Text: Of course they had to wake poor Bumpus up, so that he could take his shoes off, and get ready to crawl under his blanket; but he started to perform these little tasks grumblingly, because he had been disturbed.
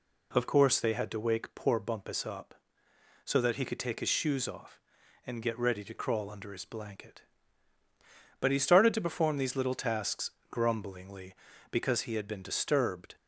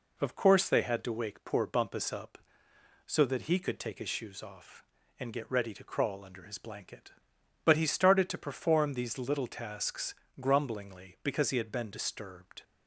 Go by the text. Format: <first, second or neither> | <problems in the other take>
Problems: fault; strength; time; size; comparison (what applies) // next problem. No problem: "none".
neither | pauses between "tasks" and "grumblingly"; slight; the same in both